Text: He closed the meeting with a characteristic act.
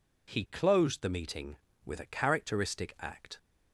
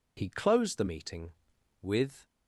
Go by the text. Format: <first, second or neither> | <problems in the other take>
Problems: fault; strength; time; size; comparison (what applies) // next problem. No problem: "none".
first | stops before "a characteristic act"; at 2.2 s